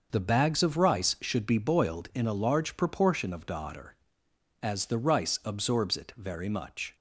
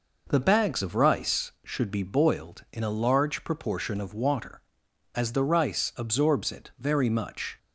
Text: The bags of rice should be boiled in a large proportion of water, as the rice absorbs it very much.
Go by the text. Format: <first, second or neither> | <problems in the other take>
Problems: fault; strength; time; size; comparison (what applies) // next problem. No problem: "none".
second | starts louder than the rest; noticeable; until 1.1 s; 6 dB // says "daughter" for "water"; at 3.4 s